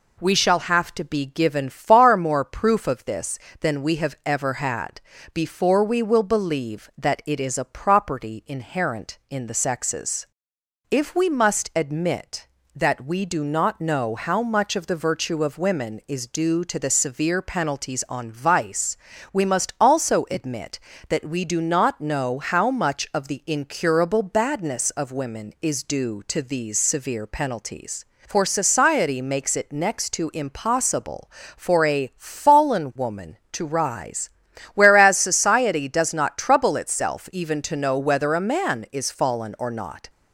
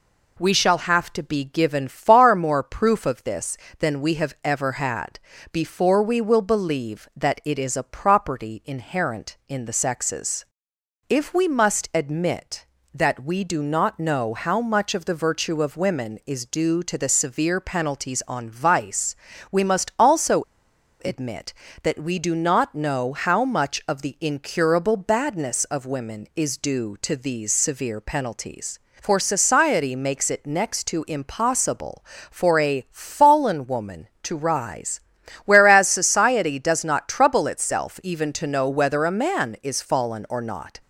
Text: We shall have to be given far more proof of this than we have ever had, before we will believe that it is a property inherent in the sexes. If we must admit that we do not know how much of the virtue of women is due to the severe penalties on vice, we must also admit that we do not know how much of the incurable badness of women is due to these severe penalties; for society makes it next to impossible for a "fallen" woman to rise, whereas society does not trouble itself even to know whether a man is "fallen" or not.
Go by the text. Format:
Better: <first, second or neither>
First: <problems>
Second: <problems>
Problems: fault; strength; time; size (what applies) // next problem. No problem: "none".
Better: first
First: none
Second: pauses between "also" and "admit"; noticeable; at 20.4 s; 0.61 s long